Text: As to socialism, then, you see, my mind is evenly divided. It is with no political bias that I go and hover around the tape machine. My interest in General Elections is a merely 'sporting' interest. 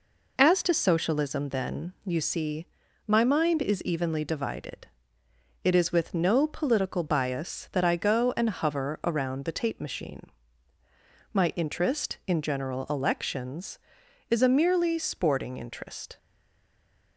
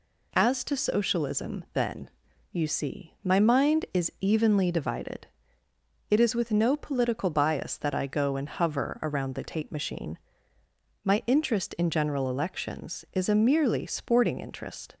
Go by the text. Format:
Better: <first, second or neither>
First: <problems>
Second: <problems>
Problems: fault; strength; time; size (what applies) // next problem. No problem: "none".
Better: second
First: stays silent after the last word; from 16.1 s on; 1.0 s long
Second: none